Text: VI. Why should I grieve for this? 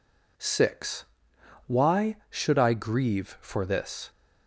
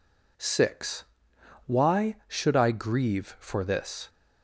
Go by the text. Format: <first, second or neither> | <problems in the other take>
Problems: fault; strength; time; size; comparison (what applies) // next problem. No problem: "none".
neither | none